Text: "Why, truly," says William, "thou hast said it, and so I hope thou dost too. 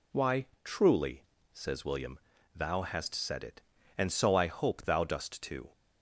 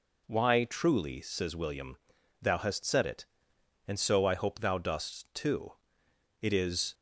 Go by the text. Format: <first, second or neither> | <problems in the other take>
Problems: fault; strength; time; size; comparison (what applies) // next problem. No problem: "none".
first | goes on to say "It is"; from 6.3 s on; 0.52 s long